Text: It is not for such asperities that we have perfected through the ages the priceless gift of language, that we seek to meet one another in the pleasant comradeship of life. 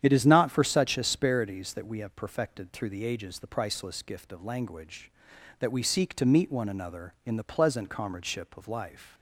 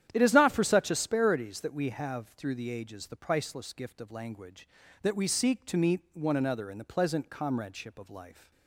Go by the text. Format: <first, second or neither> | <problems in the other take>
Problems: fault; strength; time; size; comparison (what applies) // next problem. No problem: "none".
first | starts louder than the rest; strong; until 1.1 s; 10.5 dB; strong in the first // skips "perfected"; at 2.2 s